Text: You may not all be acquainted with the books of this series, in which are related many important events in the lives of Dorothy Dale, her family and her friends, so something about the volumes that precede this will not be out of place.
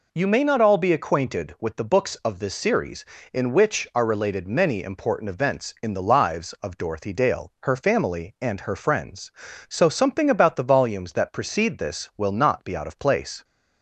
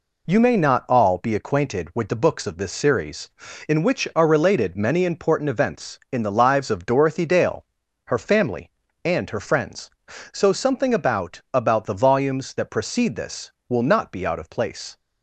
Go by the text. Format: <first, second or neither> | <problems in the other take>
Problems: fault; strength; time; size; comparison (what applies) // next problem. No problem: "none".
first | says "about" twice; at 11.5 s